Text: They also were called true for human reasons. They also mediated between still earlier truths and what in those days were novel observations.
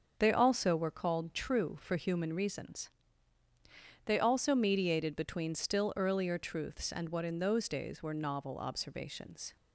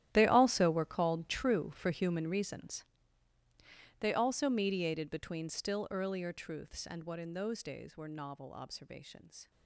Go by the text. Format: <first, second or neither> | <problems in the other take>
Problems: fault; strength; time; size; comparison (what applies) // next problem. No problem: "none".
first | gets quieter; strong; throughout; 17 dB // starts louder than the rest; strong; until 1.1 s; 13 dB; also in the first